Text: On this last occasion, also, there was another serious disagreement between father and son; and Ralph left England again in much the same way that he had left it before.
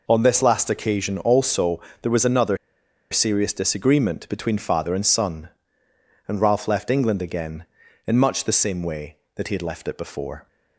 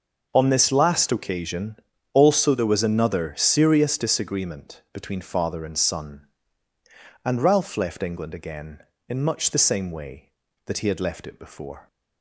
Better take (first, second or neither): second